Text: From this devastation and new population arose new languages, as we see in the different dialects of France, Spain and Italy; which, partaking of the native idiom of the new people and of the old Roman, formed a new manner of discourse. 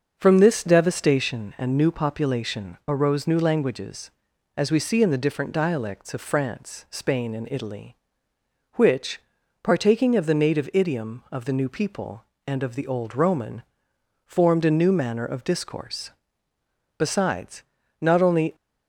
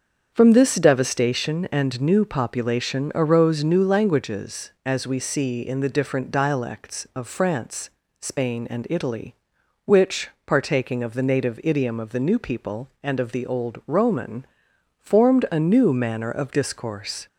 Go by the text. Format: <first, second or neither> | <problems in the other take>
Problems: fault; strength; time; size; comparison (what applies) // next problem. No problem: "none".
second | starts louder than the rest; until 1.1 s; 6.5 dB; also in the second // goes on to say "Besides not only"; from 16.9 s on; 1.5 s long